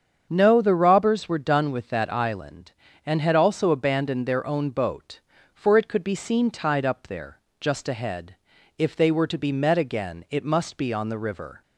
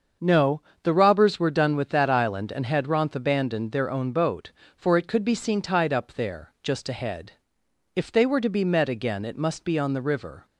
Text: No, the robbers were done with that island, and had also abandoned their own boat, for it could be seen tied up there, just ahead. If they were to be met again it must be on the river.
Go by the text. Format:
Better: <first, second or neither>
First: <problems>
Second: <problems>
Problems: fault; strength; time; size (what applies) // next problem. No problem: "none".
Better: first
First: starts louder than the rest; strong; until 1.3 s; 7.5 dB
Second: starts louder than the rest; until 1.4 s; 7 dB // says "ronth" for "also"; at 2.8 s